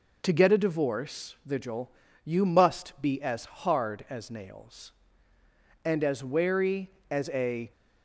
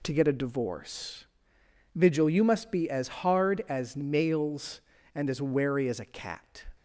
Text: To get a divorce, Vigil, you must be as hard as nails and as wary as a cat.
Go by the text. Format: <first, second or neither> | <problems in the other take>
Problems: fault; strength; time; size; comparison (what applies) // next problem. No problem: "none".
second | stops before "cat"; at 7.7 s